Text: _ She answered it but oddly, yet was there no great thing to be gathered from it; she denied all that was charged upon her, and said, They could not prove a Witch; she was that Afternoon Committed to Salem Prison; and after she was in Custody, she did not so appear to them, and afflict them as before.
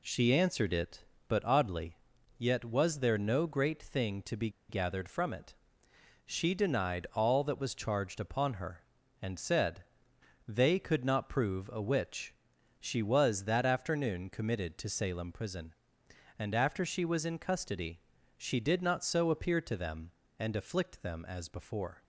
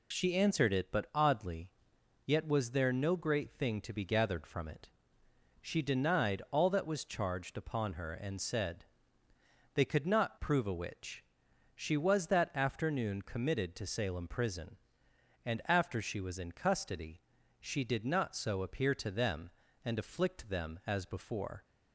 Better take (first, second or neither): second